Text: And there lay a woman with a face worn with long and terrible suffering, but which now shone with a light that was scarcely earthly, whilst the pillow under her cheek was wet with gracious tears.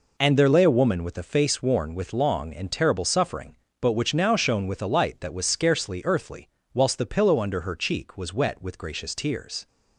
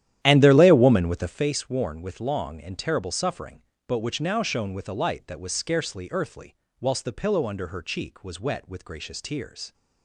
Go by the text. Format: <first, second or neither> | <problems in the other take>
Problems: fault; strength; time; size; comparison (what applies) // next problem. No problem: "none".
first | starts louder than the rest; strong; until 1.4 s; 11.5 dB